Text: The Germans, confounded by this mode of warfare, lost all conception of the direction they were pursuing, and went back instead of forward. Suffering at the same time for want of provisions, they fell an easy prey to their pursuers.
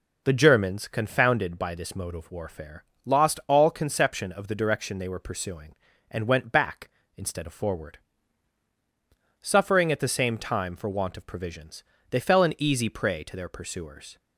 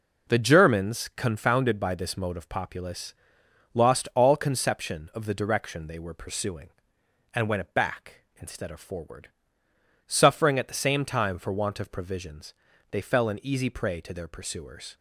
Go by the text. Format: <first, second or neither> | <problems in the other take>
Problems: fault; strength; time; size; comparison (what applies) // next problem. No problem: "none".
first | says "populace" for "warfare"; at 2.4 s